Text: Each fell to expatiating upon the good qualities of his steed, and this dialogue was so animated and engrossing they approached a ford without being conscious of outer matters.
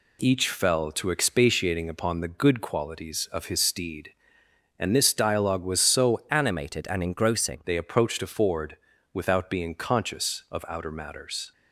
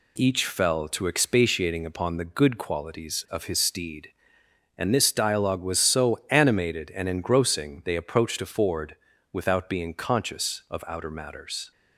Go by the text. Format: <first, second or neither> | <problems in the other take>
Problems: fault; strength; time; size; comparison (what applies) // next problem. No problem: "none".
second | changes voice from "animated" to "engrossing"; from 6.3 to 7.6 s; 1.3 s long // pauses between "ford" and "without"; slight; at 8.7 s; 0.34 s long; slight in the second